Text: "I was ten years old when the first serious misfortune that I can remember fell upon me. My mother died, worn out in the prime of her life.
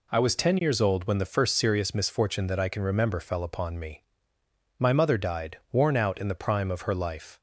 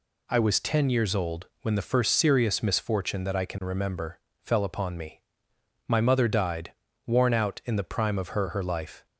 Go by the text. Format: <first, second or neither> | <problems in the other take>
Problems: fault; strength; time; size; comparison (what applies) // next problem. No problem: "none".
first | pauses between "remember" and "fell"; slight; at 4.1 s; 0.22 s long // says "her" twice; at 8.4 s